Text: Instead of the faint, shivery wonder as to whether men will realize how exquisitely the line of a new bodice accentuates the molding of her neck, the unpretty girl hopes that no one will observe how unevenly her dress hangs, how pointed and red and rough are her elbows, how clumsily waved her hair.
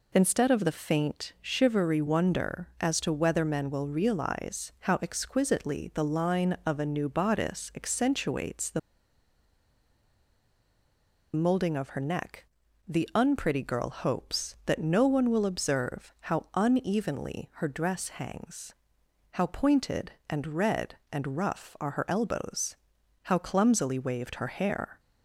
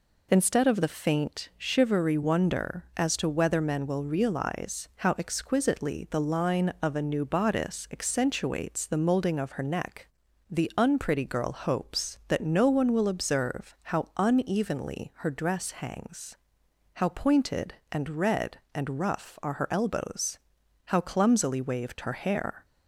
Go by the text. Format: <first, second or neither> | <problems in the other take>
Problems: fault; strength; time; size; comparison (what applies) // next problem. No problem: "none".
second | pauses between "the" and "molding"; strong; at 8.7 s; 2.5 s long